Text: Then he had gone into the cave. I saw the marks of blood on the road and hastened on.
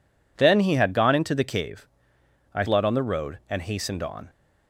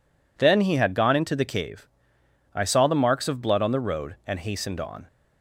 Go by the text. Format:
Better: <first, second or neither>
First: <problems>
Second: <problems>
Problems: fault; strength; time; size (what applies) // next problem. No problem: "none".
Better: second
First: skips "saw the marks of"; at 2.6 s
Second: none